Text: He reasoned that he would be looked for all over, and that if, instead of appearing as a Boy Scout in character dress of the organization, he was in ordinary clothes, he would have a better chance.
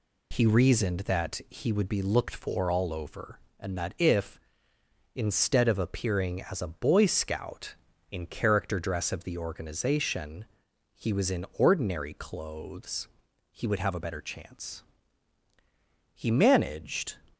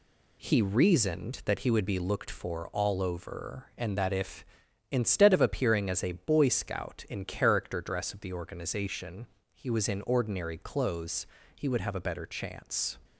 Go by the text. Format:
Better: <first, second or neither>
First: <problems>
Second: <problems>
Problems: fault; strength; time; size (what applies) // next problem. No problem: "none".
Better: second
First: goes on to say "He managed"; noticeable; from 16.1 s on; 1.0 s long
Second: none